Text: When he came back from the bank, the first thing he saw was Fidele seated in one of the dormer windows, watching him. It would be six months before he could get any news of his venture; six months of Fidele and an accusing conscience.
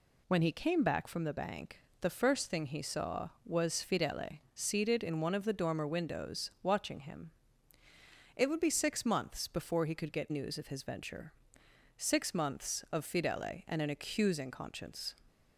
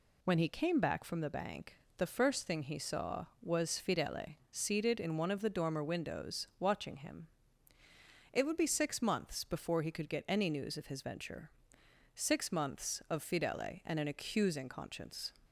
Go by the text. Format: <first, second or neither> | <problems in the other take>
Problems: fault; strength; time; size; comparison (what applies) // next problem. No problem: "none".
second | pauses between "Fidele" and "seated"; slight; at 4.3 s; 0.16 s long; slight in the second // skips "any"; at 10.2 s